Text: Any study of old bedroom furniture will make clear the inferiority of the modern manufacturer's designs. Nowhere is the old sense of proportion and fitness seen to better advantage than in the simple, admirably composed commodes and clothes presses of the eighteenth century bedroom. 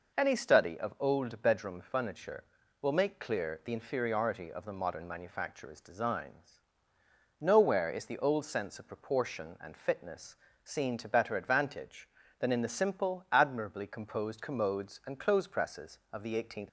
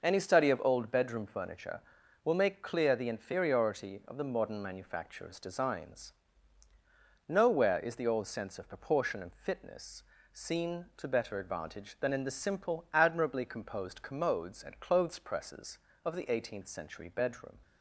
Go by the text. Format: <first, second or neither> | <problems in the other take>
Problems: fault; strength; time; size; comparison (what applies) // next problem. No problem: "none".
second | pauses between "fitness" and "seen"; slight; at 10.3 s; 0.30 s long; slight in the second // stops before "century bedroom"; at 16.6 s